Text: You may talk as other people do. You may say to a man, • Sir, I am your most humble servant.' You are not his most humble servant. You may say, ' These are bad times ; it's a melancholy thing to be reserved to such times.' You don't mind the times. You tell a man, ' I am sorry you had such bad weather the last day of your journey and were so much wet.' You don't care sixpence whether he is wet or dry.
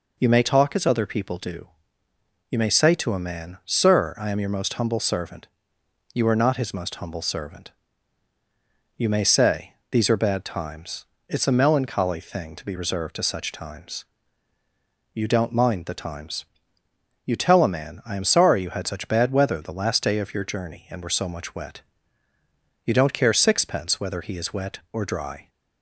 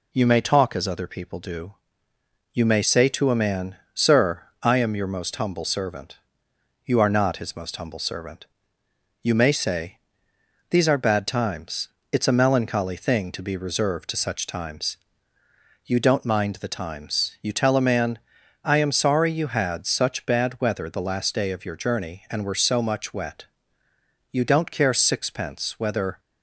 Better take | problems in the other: first | stops before "he is wet or dry"; at 26.1 s

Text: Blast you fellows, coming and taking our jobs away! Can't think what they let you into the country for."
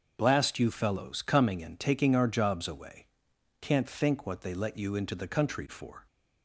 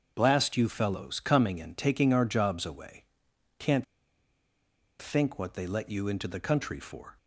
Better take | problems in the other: first | starts louder than the rest; until 1.1 s; 6.5 dB; also in the first // pauses between "Can't" and "think"; at 3.8 s; 1.1 s long

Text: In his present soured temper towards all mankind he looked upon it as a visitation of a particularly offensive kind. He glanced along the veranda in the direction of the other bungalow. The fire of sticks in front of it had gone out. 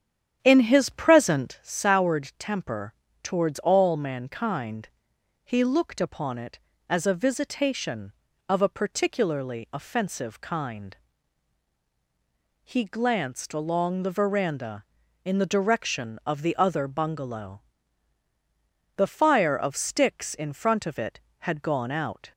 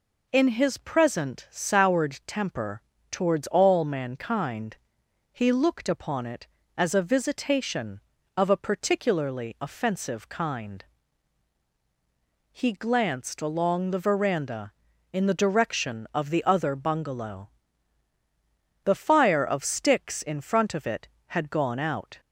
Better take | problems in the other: second | starts louder than the rest; strong; until 1.6 s; 9 dB // pauses between "temper" and "towards"; slight; at 2.9 s; 0.28 s long; slight in the second // pauses between "mankind" and "he"; noticeable; at 4.8 s; 0.56 s long; noticeable in the second

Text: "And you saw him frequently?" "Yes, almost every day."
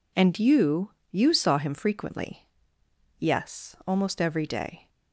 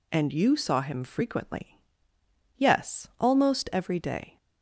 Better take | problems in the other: second | says "you" twice; at 1.1 s

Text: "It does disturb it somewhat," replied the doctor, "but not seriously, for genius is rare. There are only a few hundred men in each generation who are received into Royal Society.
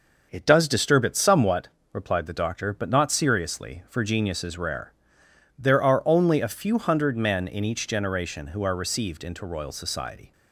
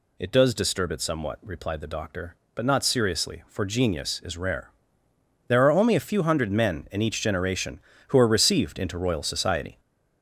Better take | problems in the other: first | gets louder; noticeable; throughout; 6 dB

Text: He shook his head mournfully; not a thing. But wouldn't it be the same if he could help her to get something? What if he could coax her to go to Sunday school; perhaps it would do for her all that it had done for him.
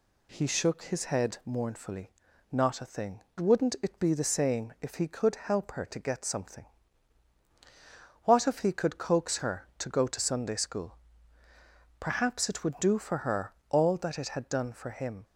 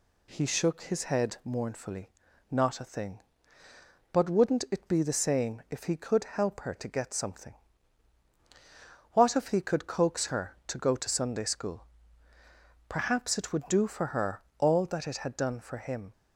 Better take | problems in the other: second | skips "But"; at 3.3 s // pauses between "her" and "all"; slight; at 13.5 s; 0.16 s long; slight in the second

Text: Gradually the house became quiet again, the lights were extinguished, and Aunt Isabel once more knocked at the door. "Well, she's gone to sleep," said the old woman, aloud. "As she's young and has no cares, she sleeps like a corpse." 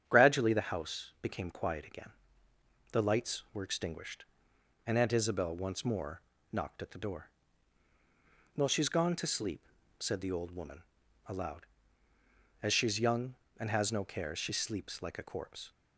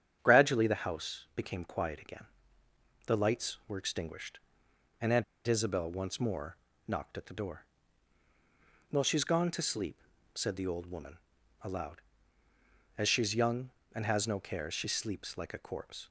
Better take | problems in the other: first | starts louder than the rest; strong; until 1.2 s; 8.5 dB; strong in the first // pauses between "Aunt" and "Isabel"; slight; at 5.2 s; 0.23 s long // pauses between "more" and "knocked"; slight; at 6.5 s; 0.32 s long; slight in the first

